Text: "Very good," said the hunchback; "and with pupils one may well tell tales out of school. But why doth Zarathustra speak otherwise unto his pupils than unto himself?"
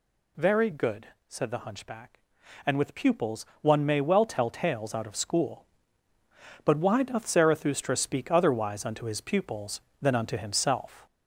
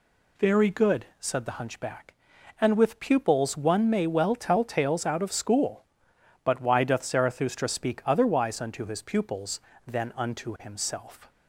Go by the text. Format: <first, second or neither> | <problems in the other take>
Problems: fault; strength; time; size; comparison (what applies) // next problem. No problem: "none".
second | gets louder; slight; throughout; 3 dB // pauses between "pupils" and "one"; slight; at 3.4 s; 0.16 s long